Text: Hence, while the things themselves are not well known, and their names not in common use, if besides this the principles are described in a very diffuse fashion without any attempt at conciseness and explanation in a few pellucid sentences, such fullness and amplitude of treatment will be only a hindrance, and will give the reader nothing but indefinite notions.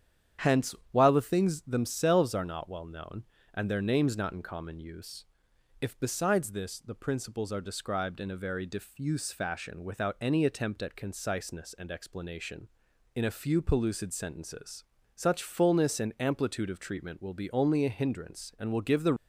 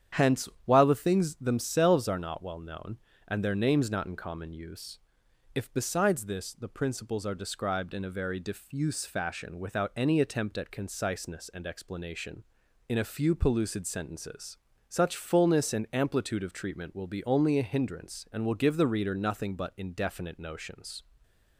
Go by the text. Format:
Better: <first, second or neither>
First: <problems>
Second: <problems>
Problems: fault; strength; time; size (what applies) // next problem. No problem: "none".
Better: second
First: starts louder than the rest; strong; until 1.5 s; 9 dB // stops before "reader nothing but indefinite notions"; at 19.1 s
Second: starts louder than the rest; strong; until 1.3 s; 9 dB